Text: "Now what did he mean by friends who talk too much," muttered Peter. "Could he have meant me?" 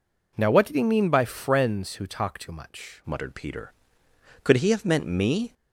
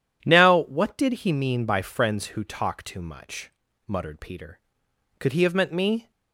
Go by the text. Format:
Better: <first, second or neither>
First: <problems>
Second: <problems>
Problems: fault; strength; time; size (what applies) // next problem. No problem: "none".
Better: second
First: changes voice at "muttered"; from 3.0 s on; 2.5 s long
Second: none